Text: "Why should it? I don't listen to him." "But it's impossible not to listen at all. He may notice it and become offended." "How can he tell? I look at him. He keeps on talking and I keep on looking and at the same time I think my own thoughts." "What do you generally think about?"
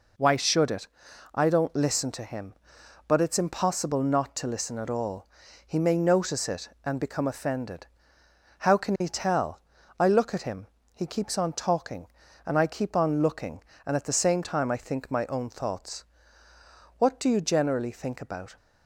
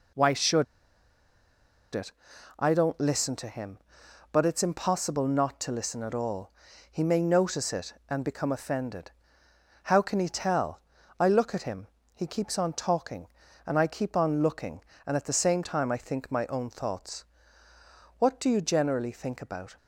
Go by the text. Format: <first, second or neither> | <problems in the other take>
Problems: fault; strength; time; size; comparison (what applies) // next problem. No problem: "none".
first | pauses between "should" and "it"; strong; at 0.6 s; 1.2 s long